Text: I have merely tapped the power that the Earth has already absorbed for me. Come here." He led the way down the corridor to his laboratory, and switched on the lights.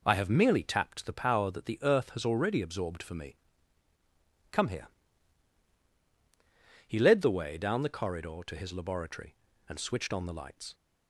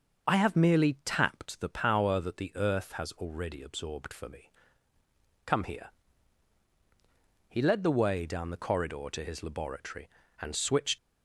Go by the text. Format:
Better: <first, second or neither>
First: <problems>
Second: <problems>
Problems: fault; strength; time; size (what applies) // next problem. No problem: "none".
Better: first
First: none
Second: starts louder than the rest; noticeable; until 1.3 s; 6 dB // stops before "on the lights"; at 10.9 s